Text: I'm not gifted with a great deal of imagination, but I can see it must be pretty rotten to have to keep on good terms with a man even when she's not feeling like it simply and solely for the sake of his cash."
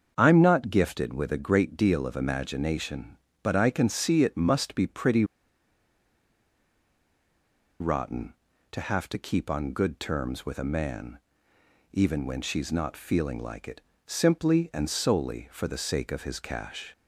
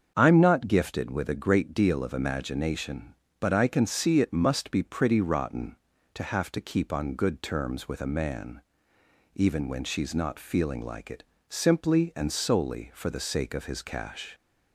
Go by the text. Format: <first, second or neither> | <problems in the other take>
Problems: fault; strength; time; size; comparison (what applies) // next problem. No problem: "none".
second | starts louder than the rest; until 1.1 s; 7 dB; also in the second // pauses between "pretty" and "rotten"; strong; at 5.2 s; 2.5 s long // pauses between "man" and "even"; noticeable; at 11.1 s; 0.78 s long; noticeable in the second // pauses between "it" and "simply"; slight; at 13.7 s; 0.24 s long; slight in the second